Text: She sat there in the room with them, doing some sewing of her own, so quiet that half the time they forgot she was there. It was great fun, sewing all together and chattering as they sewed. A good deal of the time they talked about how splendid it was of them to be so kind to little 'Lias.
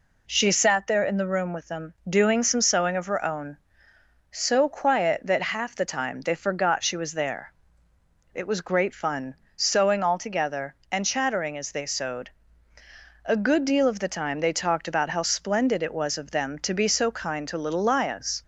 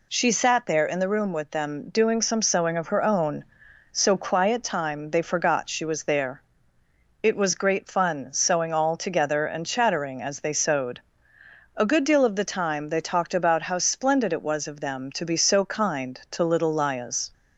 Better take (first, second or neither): first